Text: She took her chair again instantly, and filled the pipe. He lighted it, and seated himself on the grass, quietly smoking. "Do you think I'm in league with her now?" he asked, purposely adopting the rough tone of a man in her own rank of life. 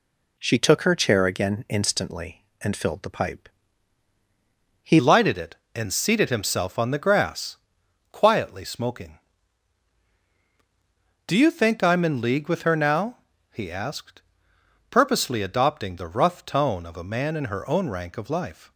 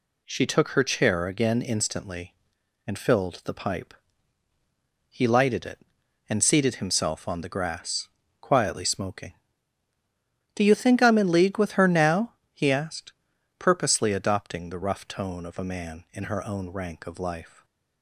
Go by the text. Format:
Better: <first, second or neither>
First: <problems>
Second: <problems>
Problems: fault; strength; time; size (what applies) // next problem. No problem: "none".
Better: second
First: changes voice at "lighted"; from 4.9 s on; 13.8 s long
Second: none